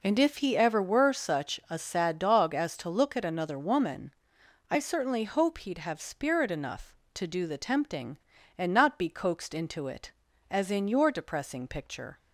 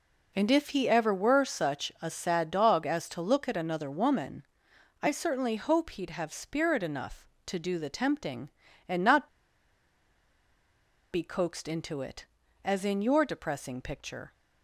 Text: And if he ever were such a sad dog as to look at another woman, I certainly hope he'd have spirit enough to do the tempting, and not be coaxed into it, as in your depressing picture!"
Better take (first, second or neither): first